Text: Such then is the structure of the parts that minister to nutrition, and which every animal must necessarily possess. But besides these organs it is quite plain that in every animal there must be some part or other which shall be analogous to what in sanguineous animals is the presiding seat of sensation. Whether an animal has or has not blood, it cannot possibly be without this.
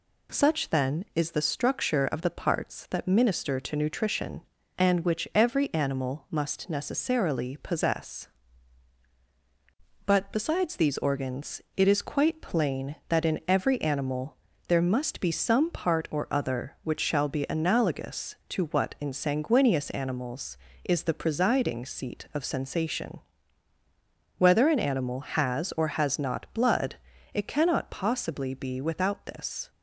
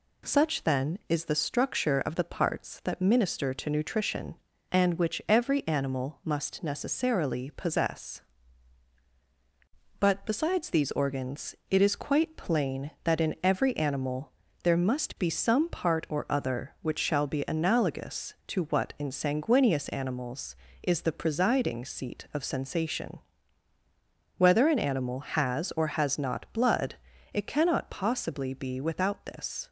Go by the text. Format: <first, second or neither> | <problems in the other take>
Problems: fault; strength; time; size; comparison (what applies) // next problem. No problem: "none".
neither | pauses between "organs" and "it"; slight; the same in both // pauses between "animal" and "there"; slight; the same in both